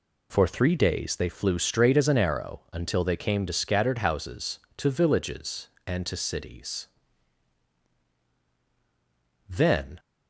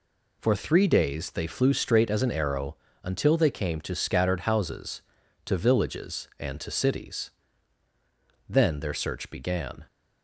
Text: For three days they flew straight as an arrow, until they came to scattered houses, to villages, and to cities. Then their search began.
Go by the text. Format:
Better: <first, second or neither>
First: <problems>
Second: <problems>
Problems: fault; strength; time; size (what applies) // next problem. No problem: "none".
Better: second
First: stops before "their search began"; at 9.9 s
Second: none